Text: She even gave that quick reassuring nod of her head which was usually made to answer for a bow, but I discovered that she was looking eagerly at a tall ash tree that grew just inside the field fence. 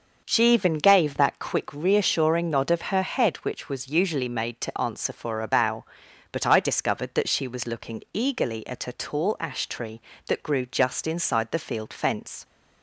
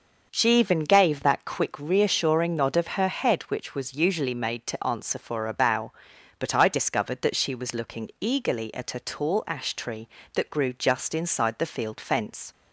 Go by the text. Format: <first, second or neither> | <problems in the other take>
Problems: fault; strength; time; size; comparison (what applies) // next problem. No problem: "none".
neither | starts louder than the rest; the same in both